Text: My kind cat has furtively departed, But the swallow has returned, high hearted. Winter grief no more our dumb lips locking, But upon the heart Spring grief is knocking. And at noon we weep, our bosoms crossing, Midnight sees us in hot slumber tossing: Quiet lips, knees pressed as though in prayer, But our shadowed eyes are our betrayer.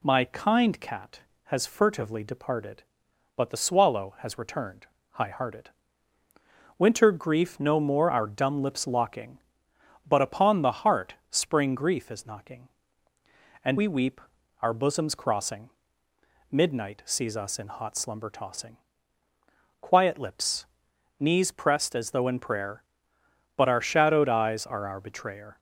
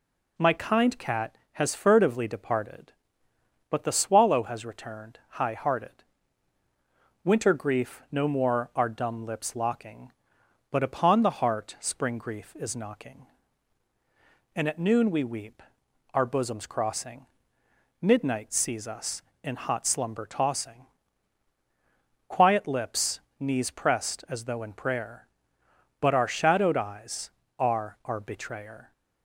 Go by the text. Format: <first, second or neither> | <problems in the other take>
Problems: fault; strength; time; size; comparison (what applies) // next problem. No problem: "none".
second | pauses between "heart" and "Spring"; slight; at 11.1 s; 0.16 s long // skips "at noon"; at 13.7 s